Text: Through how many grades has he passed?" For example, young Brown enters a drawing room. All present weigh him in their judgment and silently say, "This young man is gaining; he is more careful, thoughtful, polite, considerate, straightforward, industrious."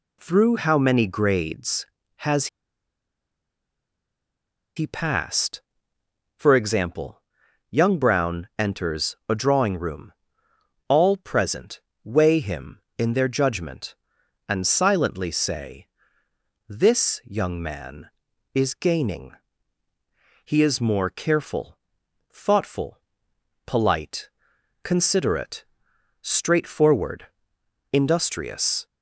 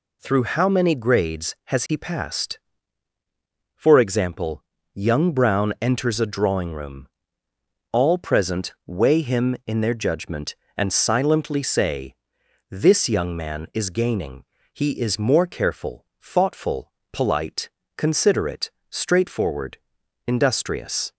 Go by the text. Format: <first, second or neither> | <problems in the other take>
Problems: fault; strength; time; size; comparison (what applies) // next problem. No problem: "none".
second | pauses between "has" and "he"; strong; at 2.4 s; 2.3 s long // pauses between "present" and "weigh"; slight; at 11.7 s; 0.24 s long